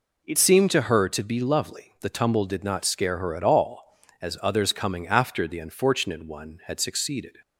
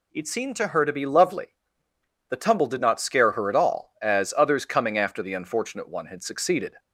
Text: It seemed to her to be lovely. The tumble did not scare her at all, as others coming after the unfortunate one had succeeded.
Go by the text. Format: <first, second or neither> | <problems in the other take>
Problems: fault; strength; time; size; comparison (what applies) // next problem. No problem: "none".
second | changes voice at "seemed"; from 0.3 s on; 7.0 s long